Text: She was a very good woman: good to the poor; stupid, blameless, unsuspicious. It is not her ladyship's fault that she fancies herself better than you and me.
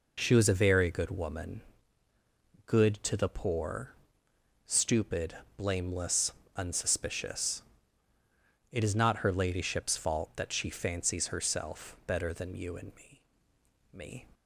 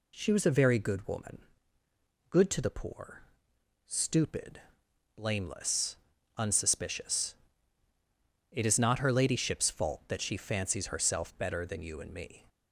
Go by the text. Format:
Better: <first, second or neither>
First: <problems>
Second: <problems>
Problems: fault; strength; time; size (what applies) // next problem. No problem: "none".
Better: second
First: says "me" twice; at 13.9 s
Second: none